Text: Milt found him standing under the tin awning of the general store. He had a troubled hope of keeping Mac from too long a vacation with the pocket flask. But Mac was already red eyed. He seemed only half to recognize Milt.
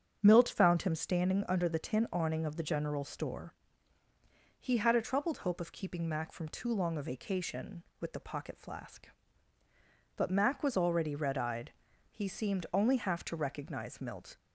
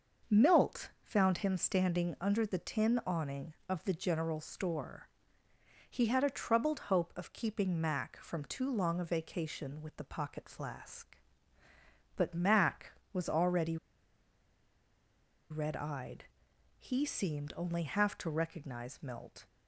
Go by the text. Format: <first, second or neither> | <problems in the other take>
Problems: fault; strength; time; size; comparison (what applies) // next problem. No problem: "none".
first | starts louder than the rest; until 1.4 s; 6 dB; strong in the first // pauses between "already" and "red"; strong; at 13.7 s; 1.7 s long